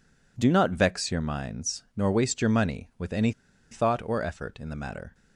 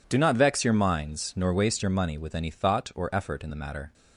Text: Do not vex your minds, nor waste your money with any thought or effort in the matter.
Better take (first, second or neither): second